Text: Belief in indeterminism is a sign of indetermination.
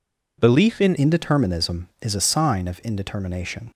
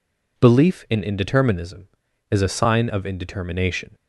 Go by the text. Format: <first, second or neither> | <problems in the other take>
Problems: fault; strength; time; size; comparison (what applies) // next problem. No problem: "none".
second | changes voice at "indeterminism"; from 0.9 s on; 2.8 s long